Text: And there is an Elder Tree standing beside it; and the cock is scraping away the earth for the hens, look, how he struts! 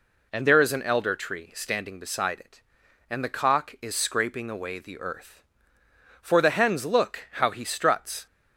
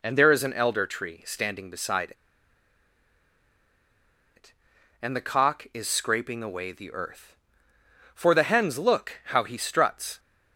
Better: first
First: none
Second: pauses between "beside" and "it"; strong; at 2.1 s; 2.2 s long

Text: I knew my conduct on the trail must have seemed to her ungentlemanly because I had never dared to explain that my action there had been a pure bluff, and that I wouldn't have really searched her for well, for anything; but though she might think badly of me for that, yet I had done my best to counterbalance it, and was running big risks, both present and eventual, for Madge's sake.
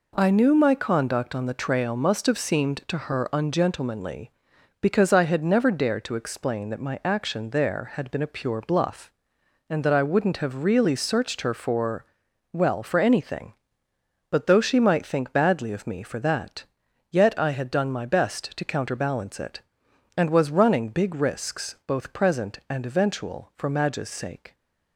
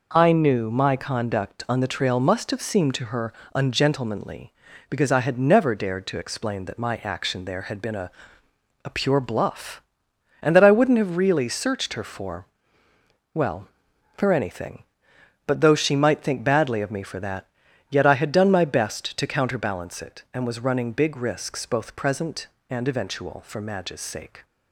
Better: first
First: pauses between "for" and "well"; noticeable; at 12.0 s; 0.48 s long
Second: pauses between "her" and "ungentlemanly"; slight; at 3.3 s; 0.24 s long // says "a" twice; at 8.8 s // pauses between "for" and "well"; noticeable; at 12.4 s; 0.88 s long

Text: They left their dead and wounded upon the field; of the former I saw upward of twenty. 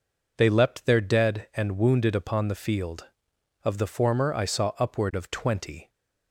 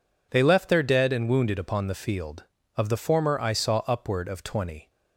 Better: second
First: says "leapt" for "left"; at 0.4 s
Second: none

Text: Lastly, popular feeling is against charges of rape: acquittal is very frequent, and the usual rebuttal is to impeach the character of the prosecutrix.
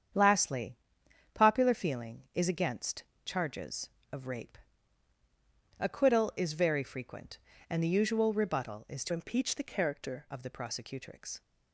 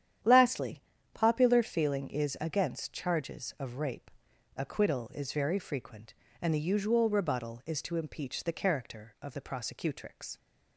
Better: second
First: starts louder than the rest; strong; until 1.7 s; 8 dB // pauses between "against" and "charges"; slight; at 3.0 s; 0.20 s long // changes voice from "impeach" to "character"; from 9.1 to 10.2 s; 1.1 s long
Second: starts louder than the rest; strong; until 1.5 s; 9.5 dB

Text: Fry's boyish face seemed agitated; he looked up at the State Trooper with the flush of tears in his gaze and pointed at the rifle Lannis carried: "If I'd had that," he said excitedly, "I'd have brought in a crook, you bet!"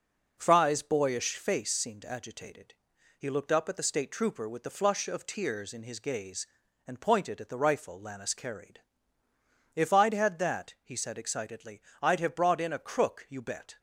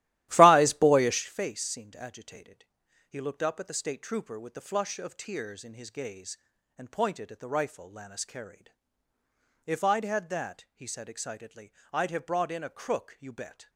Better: first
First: none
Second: starts louder than the rest; strong; until 1.2 s; 14.5 dB

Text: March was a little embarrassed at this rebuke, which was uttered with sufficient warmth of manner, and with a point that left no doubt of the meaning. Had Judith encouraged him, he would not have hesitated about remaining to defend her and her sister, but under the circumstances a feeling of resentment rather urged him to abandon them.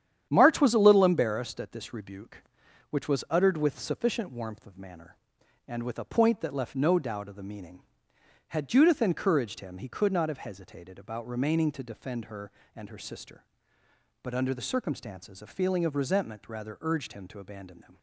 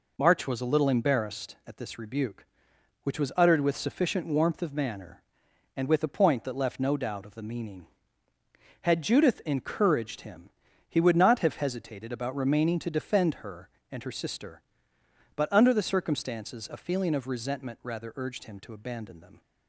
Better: second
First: starts louder than the rest; strong; until 1.3 s; 9.5 dB // says "could" for "would"; at 9.8 s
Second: none

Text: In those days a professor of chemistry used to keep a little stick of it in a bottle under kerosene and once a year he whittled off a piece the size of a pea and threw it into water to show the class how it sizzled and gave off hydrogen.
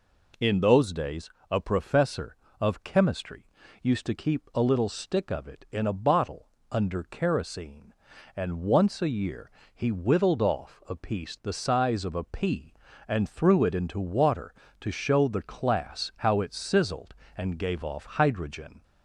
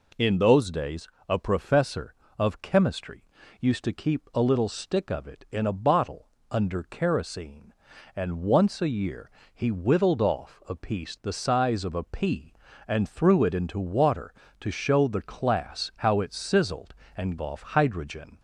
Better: first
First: pauses between "days" and "a"; slight; at 1.2 s; 0.22 s long // pauses between "chemistry" and "used"; slight; at 3.4 s; 0.36 s long // pauses between "bottle" and "under"; slight; at 6.4 s; 0.22 s long // pauses between "year" and "he"; slight; at 9.5 s; 0.24 s long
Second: pauses between "days" and "a"; slight; at 1.0 s; 0.22 s long // pauses between "chemistry" and "used"; slight; at 3.2 s; 0.36 s long // pauses between "bottle" and "under"; slight; at 6.2 s; 0.22 s long // pauses between "year" and "he"; slight; at 9.3 s; 0.24 s long // skips "gave"; at 17.3 s

